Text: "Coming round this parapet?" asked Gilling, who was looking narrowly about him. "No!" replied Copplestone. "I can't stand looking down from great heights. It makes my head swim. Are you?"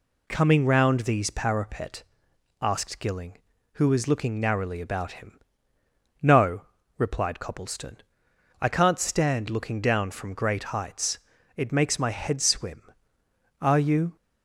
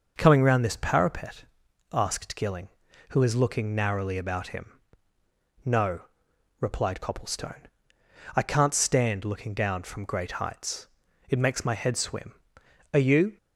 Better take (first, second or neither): second